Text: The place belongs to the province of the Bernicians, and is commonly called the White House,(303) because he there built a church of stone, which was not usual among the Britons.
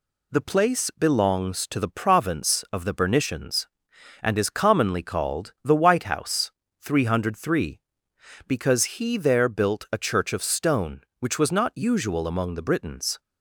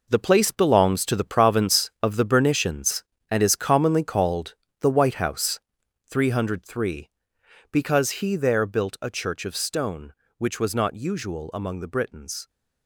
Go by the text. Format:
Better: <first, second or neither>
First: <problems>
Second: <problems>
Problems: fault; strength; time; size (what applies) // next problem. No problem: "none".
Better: first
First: none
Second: gets quieter; strong; throughout; 9.5 dB // pauses between "called" and "the"; slight; at 4.5 s; 0.26 s long